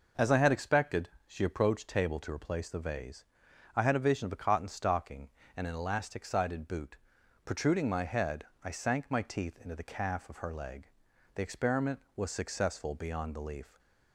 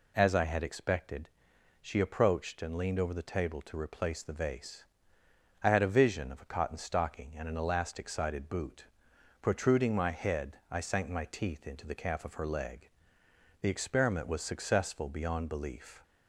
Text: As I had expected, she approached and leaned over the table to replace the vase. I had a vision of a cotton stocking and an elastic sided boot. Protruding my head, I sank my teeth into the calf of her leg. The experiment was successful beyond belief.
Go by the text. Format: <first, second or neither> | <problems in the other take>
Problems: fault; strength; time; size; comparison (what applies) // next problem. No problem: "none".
second | skips "and leaned over the"; at 1.8 s